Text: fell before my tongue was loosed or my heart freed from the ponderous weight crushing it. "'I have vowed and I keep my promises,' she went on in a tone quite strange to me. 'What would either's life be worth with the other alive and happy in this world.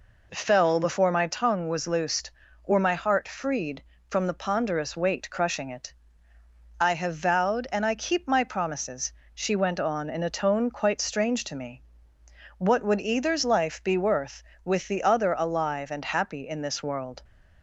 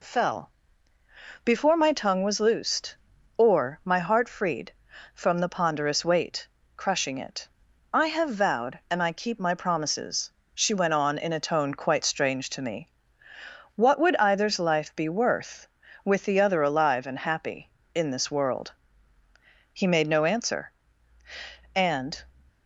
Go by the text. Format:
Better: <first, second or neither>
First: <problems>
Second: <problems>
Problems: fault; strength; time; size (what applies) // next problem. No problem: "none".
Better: first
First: none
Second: pauses between "fell" and "before"; noticeable; at 0.5 s; 0.94 s long // pauses between "weight" and "crushing"; slight; at 6.4 s; 0.28 s long // goes on to say "He made no answer and"; strong; from 19.7 s on; 2.4 s long